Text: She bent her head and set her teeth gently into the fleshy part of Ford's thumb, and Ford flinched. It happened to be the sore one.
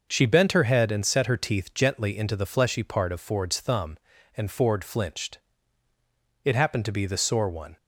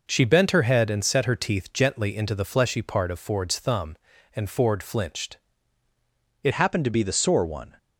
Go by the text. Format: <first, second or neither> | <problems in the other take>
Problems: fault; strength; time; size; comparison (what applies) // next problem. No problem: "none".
first | changes voice at "happened"; from 6.5 s on; 1.2 s long